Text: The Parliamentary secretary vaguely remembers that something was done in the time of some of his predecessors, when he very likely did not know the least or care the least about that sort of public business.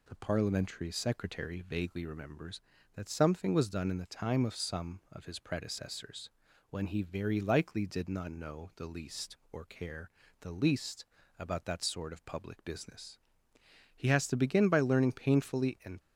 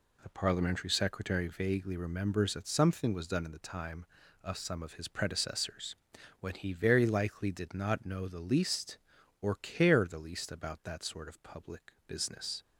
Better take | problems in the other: second | pauses between "care" and "the"; slight; at 10.0 s; 0.32 s long // pauses between "least" and "about"; slight; at 11.0 s; 0.32 s long // goes on to say "He has to begin by learning painfully and"; strong; from 13.9 s on; 2.0 s long

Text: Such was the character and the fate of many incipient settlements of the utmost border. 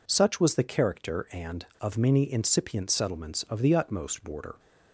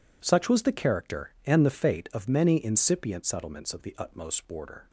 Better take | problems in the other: second | skips "the fate"; at 1.7 s

